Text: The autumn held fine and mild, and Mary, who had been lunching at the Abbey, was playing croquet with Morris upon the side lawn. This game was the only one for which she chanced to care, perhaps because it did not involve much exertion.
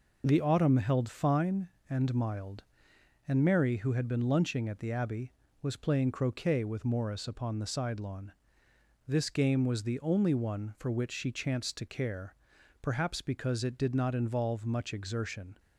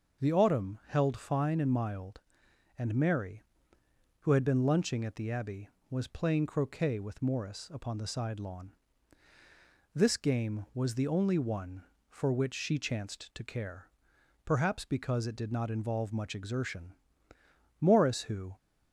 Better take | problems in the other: first | starts louder than the rest; noticeable; until 1.3 s; 6 dB // goes on to say "Morris who"; noticeable; from 17.8 s on; 0.74 s long

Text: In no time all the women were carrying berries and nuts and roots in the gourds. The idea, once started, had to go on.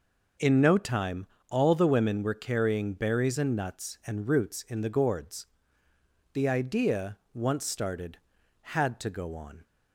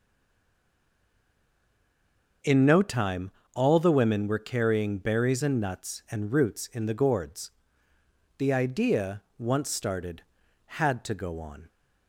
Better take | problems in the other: first | stays silent before the first word; until 2.4 s; 2.4 s long // pauses between "time" and "all"; slight; at 3.2 s; 0.24 s long; slight in the first

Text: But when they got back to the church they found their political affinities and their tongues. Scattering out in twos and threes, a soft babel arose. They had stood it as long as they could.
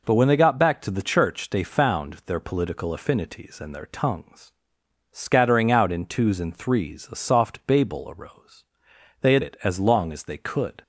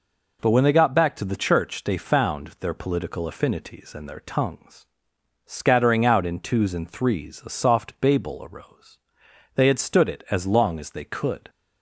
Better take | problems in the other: second | skips "stood"; at 9.4 s

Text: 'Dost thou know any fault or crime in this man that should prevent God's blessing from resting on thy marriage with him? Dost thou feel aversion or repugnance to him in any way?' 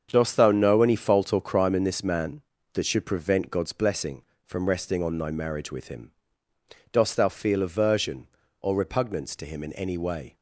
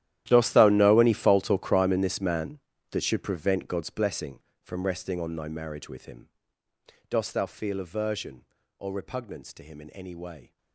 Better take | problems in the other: first | gets quieter; strong; throughout; 19 dB // starts louder than the rest; strong; until 1.2 s; 12.5 dB; strong in the first

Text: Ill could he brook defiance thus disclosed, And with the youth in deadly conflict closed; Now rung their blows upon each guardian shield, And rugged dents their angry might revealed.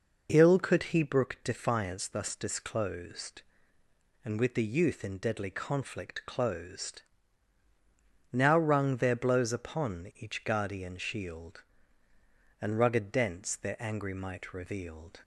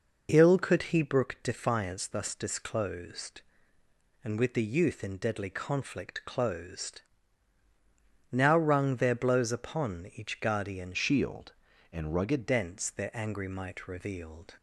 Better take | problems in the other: first | changes voice from "shield" to "rugged"; from 10.9 to 12.4 s; 1.5 s long

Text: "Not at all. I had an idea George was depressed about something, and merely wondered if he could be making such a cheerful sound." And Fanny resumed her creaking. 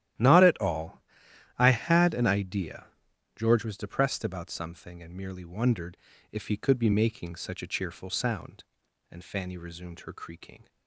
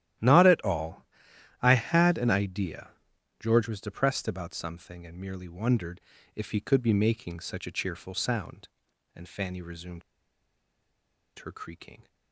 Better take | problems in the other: first | starts louder than the rest; strong; until 1.7 s; 12.5 dB; strong in the first // pauses between "idea" and "George"; noticeable; at 2.9 s; 0.48 s long; noticeable in the first // pauses between "wondered" and "if"; slight; at 6.0 s; 0.34 s long; slight in the first // pauses between "resumed" and "her"; strong; at 10.0 s; 1.3 s long

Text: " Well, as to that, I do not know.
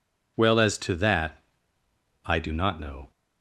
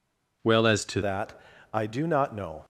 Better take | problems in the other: first | changes voice at "that"; from 1.0 s on; 1.6 s long

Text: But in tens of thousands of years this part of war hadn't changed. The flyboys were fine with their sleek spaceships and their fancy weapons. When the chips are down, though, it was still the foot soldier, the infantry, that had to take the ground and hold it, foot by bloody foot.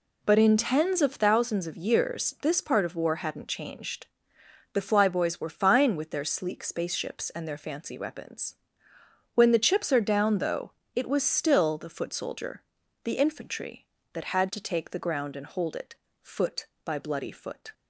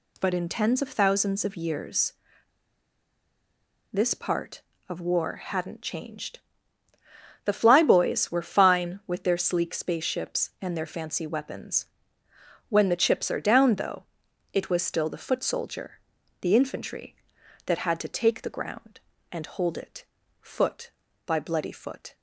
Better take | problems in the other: first | pauses between "years" and "this"; strong; at 2.1 s; 1.7 s long

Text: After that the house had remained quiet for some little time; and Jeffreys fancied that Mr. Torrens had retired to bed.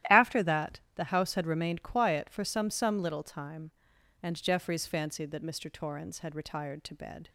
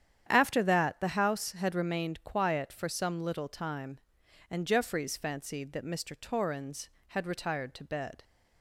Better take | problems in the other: second | starts louder than the rest; strong; until 1.2 s; 13 dB; strong in the second // says "some" twice; at 2.6 s

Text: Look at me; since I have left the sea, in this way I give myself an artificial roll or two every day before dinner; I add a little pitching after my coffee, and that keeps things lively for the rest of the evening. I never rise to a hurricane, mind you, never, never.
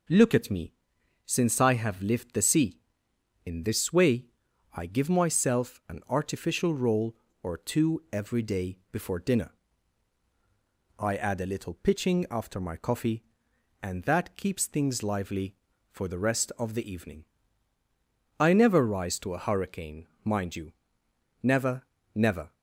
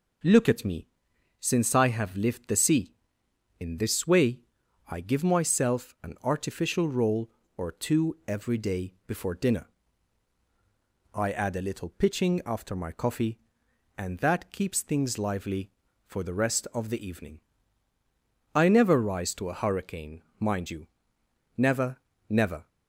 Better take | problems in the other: neither | pauses between "way" and "I"; noticeable; the same in both

